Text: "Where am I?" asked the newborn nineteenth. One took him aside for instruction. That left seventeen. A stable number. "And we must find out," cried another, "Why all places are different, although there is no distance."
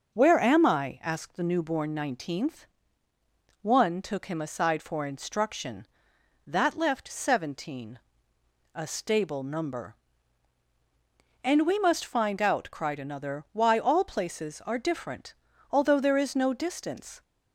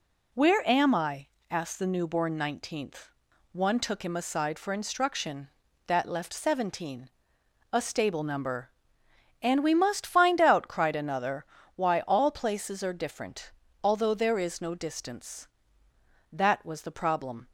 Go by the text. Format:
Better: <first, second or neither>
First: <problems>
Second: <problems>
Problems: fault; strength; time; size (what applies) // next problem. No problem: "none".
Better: first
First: none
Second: goes on to say "That was the problem"; noticeable; from 16.3 s on; 1.1 s long